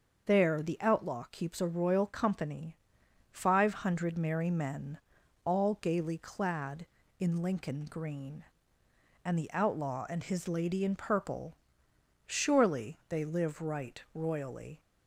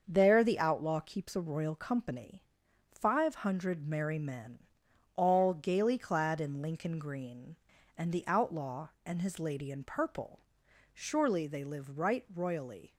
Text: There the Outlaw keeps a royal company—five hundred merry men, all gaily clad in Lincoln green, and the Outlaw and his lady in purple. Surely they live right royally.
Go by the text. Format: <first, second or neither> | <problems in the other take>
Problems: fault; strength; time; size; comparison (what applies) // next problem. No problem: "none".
neither | starts louder than the rest; the same in both